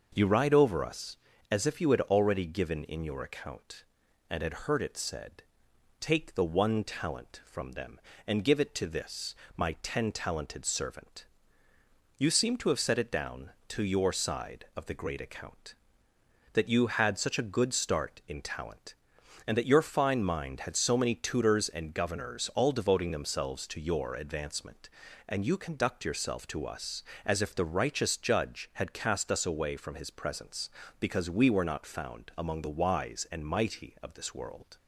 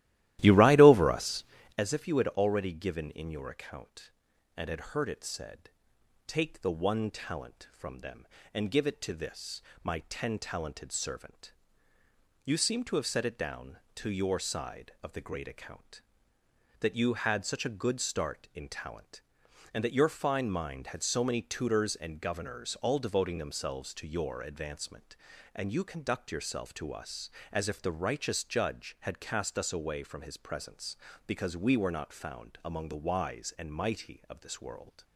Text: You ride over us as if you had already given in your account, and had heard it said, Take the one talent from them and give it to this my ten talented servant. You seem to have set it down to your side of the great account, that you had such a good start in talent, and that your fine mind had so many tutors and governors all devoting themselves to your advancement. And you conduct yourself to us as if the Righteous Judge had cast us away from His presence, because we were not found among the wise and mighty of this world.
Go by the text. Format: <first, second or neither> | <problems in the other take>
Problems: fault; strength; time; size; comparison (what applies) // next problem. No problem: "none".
first | starts louder than the rest; strong; until 1.8 s; 15 dB // pauses between "this" and "my"; slight; at 9.5 s; 0.24 s long; slight in the first